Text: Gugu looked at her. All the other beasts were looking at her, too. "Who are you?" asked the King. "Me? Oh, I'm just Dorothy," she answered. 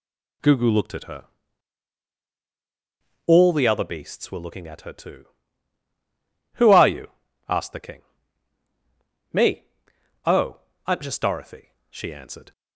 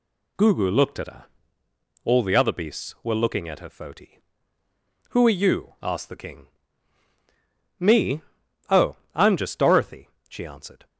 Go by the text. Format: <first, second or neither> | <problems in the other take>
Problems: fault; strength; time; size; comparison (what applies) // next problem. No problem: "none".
first | says "foti" for "too"; at 3.6 s